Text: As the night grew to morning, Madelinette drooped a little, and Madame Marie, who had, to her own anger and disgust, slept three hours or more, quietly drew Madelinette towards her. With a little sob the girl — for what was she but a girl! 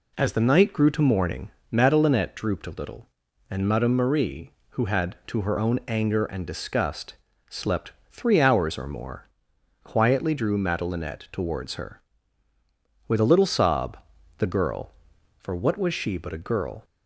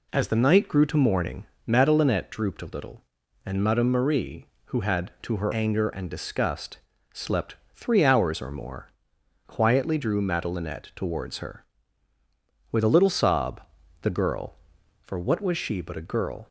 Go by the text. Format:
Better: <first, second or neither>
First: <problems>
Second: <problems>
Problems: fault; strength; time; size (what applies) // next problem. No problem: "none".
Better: first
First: pauses between "slept" and "three"; slight; at 7.9 s; 0.18 s long // pauses between "sob" and "the"; at 13.9 s; 0.38 s long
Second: skips "own"; at 5.5 s // pauses between "slept" and "three"; slight; at 7.5 s; 0.18 s long // pauses between "sob" and "the"; at 13.6 s; 0.38 s long